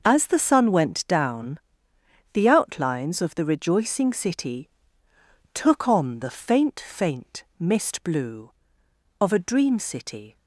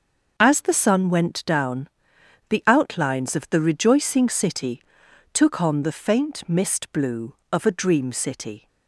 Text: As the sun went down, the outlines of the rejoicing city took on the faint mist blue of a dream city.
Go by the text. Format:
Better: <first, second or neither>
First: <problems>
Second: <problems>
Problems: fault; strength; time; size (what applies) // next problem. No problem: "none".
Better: second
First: starts louder than the rest; noticeable; until 1.0 s; 6 dB // pauses between "city" and "took"; noticeable; at 4.6 s; 0.86 s long // says "faint" twice; at 6.7 s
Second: starts louder than the rest; until 1.3 s; 6.5 dB // pauses between "city" and "took"; noticeable; at 4.8 s; 0.50 s long